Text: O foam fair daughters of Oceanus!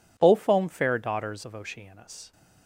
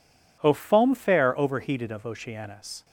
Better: first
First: none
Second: says "overheated" for "daughters"; at 1.3 s

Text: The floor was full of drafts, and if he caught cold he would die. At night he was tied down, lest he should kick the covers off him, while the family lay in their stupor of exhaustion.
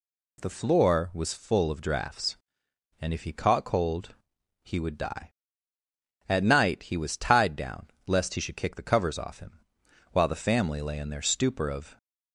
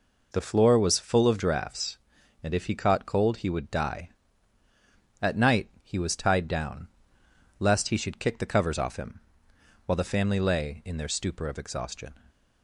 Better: second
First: pauses between "cold" and "he"; noticeable; at 4.1 s; 0.48 s long // stops before "exhaustion"; at 11.9 s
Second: none

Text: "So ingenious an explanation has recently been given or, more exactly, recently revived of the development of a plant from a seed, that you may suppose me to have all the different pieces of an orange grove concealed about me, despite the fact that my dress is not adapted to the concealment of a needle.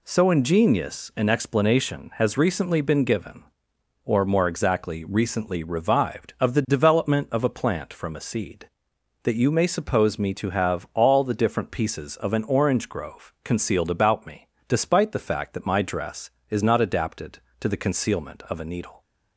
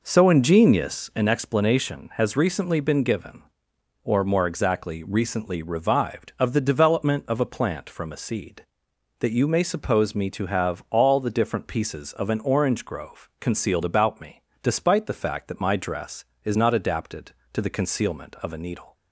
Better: first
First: none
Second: starts louder than the rest; noticeable; until 1.4 s; 5 dB

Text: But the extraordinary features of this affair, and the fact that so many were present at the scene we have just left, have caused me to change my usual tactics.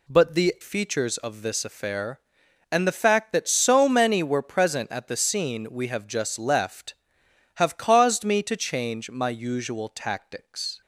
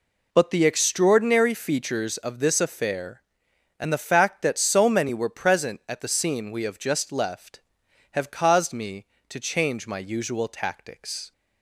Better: second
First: skips "extraordinary"; at 0.5 s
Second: none

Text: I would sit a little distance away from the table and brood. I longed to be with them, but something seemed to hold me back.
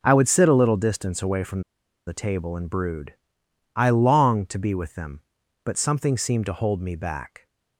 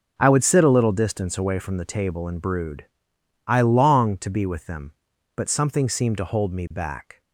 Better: second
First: pauses between "from" and "the"; noticeable; at 1.6 s; 0.46 s long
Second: none

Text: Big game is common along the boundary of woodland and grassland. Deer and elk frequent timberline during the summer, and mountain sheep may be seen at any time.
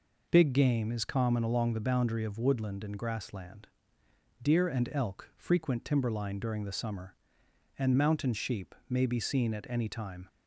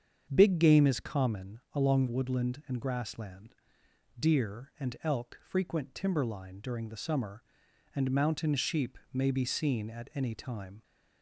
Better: first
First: none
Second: starts louder than the rest; strong; until 1.3 s; 7.5 dB // skips "the boundary of"; at 2.0 s // pauses between "sheep" and "may"; slight; at 8.9 s; 0.16 s long

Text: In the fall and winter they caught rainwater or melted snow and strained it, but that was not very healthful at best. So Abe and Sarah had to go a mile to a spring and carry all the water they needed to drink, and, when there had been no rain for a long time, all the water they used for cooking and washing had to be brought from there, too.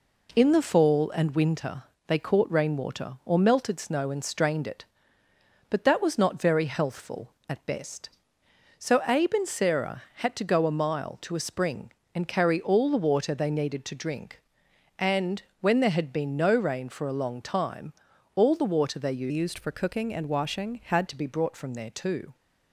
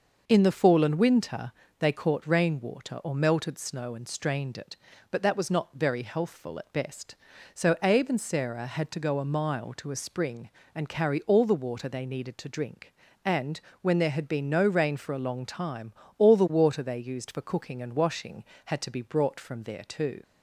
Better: second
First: pauses between "winter" and "they"; slight; at 1.8 s; 0.24 s long // changes voice from "used" to "had"; from 19.2 to 21.0 s; 1.8 s long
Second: pauses between "winter" and "they"; slight; at 1.5 s; 0.26 s long

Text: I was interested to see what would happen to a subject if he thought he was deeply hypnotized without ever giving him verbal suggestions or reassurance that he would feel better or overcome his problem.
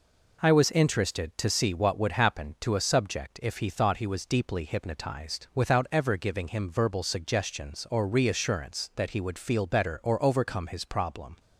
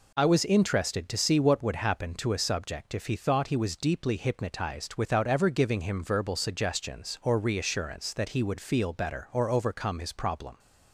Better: neither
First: none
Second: none

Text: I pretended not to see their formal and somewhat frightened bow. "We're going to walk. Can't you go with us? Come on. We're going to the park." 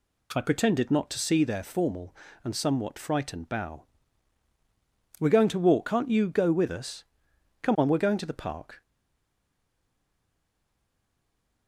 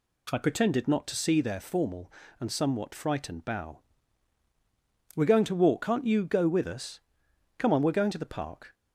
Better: second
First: stays silent after the last word; strong; from 8.8 s on; 2.8 s long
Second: none

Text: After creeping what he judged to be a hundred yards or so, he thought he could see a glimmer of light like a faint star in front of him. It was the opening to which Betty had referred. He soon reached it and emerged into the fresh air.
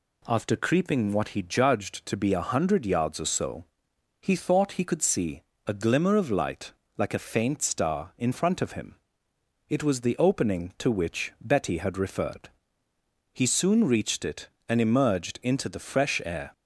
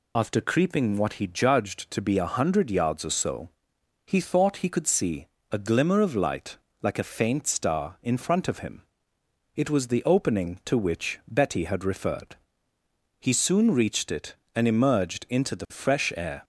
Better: first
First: pauses between "see" and "a"; slight; at 5.4 s; 0.26 s long // pauses between "light" and "like"; slight; at 6.7 s; 0.26 s long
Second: loses the start of "After"; at 0.1 s; 70 ms // pauses between "see" and "a"; slight; at 5.2 s; 0.26 s long // pauses between "light" and "like"; slight; at 6.5 s; 0.26 s long

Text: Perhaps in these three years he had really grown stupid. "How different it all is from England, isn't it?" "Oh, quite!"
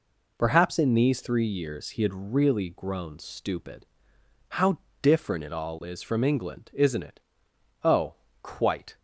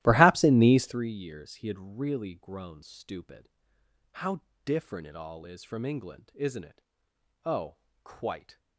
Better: first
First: pauses between "How" and "different"; slight; at 4.7 s; 0.24 s long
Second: starts louder than the rest; strong; until 1.1 s; 15 dB // pauses between "How" and "different"; slight; at 4.4 s; 0.24 s long

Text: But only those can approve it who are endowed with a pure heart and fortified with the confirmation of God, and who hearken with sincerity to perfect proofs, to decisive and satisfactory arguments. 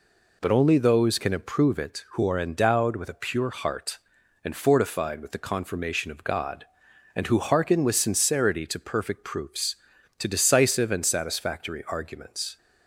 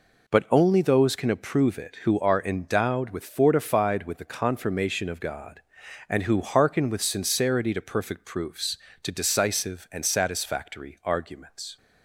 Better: first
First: none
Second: skips "a pure heart and"; at 3.2 s

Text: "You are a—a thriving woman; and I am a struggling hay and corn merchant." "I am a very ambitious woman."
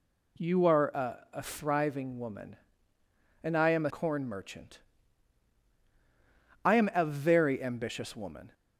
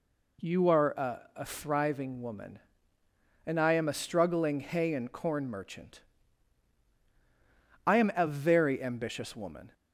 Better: second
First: skips "struggling hay and"; at 3.9 s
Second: none

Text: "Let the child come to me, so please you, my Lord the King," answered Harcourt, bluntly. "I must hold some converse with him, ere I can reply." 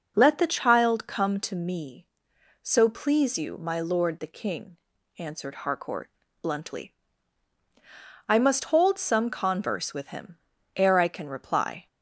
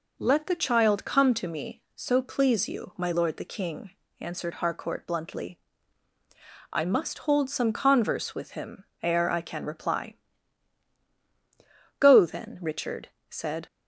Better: first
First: none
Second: goes on to say "Go then Richard said"; strong; from 11.9 s on; 1.6 s long

